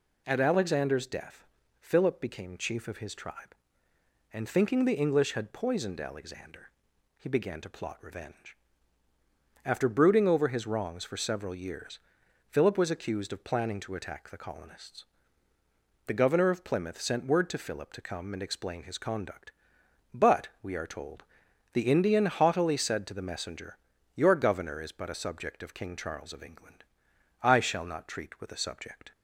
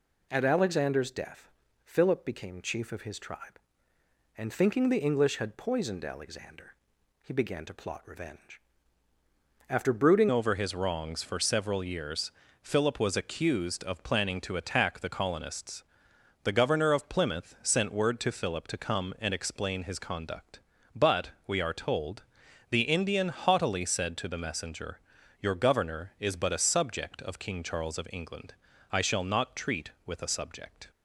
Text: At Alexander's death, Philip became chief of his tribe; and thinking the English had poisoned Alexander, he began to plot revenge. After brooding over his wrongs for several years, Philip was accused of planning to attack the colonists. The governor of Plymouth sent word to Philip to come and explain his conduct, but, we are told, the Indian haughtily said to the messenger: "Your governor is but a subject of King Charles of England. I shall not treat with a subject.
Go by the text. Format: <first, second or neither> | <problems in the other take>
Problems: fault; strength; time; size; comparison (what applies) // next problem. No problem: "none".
first | changes voice at "over"; from 10.2 s on; 20.7 s long